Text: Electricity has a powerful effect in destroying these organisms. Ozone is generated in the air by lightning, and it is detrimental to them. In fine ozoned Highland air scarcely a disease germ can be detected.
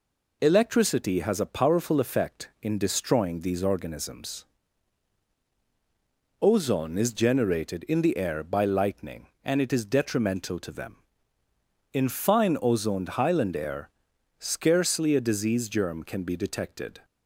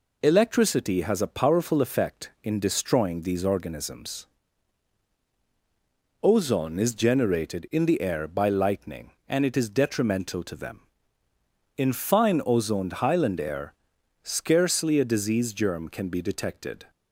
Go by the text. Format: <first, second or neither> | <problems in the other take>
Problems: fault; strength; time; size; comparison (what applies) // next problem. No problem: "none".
neither | pauses between "air" and "scarcely"; noticeable; the same in both